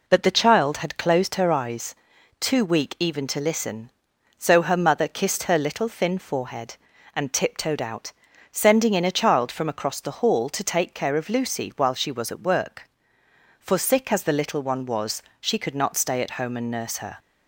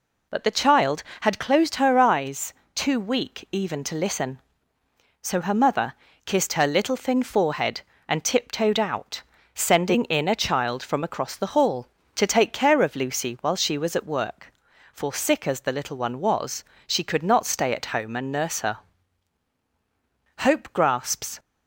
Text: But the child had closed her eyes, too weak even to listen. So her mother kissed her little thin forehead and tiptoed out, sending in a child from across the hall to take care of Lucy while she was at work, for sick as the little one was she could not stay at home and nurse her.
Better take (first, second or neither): first